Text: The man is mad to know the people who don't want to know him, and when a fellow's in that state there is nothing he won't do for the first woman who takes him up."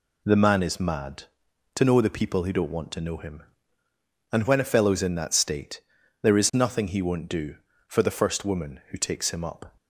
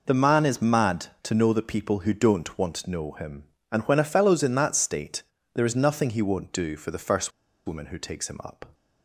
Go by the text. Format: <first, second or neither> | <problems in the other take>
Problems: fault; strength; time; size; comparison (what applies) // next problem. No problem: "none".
first | pauses between "state" and "there"; slight; at 5.2 s; 0.32 s long; also in the first // pauses between "first" and "woman"; at 7.3 s; 0.37 s long